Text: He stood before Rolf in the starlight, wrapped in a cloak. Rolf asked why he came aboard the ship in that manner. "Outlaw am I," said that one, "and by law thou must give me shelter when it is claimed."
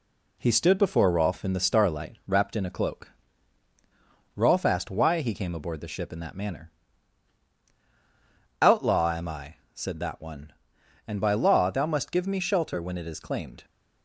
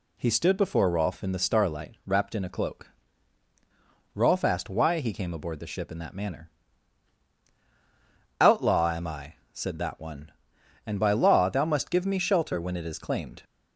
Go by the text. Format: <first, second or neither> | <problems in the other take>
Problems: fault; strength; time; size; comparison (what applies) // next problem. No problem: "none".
second | gets quieter; slight; throughout; 2.5 dB